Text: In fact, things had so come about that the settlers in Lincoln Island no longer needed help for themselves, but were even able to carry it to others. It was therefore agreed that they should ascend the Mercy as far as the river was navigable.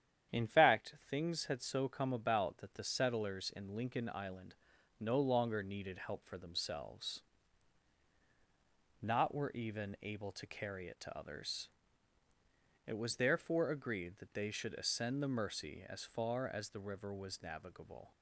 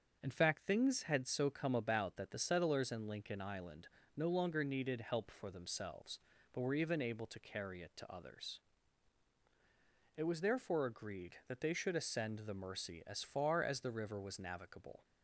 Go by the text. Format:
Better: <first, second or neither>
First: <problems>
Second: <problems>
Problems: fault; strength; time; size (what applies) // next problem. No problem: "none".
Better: second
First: starts louder than the rest; strong; until 1.4 s; 9.5 dB // pauses between "Island" and "no"; noticeable; at 4.5 s; 0.46 s long // says "not" for "but"; at 9.0 s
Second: starts louder than the rest; until 1.2 s; 7 dB // pauses between "Island" and "no"; slight; at 3.8 s; 0.30 s long